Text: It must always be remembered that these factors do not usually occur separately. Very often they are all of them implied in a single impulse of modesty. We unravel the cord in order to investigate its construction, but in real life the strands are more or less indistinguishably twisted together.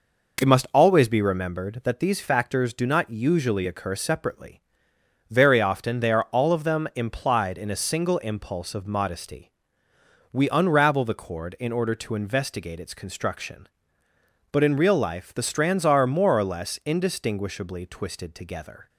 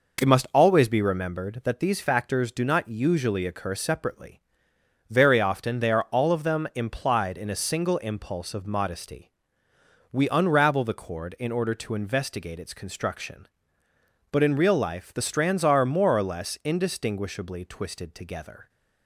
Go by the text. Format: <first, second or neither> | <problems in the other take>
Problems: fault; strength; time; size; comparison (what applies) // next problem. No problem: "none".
neither | none